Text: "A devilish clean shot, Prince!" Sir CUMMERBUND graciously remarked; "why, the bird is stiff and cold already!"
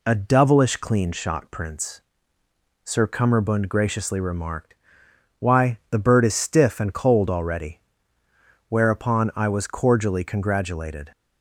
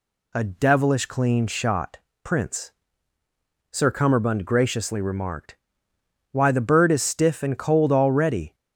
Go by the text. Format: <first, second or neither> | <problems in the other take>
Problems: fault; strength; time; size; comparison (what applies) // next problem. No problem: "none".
second | goes on to say "Whereupon I was cordially congratulated"; strong; from 8.6 s on; 2.4 s long